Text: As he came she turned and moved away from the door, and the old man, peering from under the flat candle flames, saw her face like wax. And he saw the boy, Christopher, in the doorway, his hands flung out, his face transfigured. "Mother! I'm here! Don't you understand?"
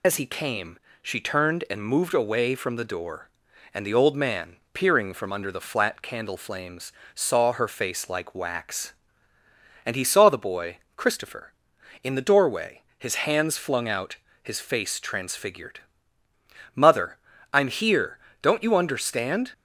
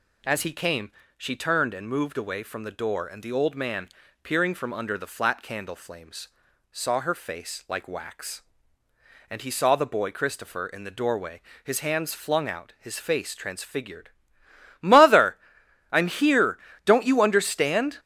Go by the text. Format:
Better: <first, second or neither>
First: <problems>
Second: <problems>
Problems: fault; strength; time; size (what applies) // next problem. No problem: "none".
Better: second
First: loses the start of "As"; at 0.0 s; 45 ms // pauses between "came" and "she"; slight; at 0.7 s; 0.24 s long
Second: pauses between "came" and "she"; slight; at 0.9 s; 0.26 s long